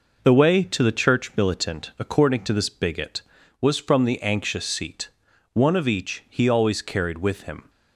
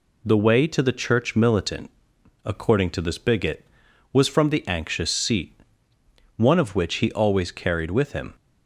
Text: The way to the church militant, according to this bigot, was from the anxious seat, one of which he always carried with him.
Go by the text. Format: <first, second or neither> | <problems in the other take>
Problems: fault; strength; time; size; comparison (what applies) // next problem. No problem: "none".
second | says "each" for "which"; at 5.8 s